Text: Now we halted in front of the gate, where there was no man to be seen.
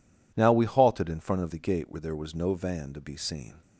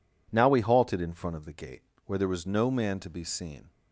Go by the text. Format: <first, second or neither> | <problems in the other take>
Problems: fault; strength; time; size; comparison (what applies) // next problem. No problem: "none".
second | says "van" for "man"; at 2.5 s